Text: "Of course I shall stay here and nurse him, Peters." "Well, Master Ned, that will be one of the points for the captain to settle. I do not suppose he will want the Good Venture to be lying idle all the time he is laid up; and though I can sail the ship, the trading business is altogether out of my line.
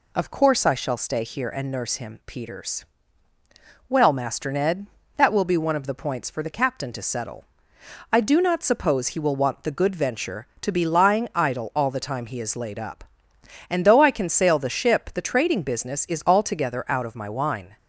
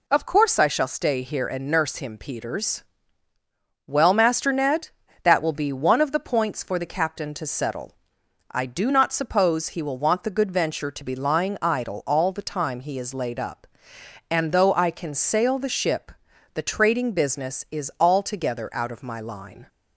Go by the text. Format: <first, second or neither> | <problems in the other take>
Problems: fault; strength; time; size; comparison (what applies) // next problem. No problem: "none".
second | says "wine" for "line"; at 17.2 s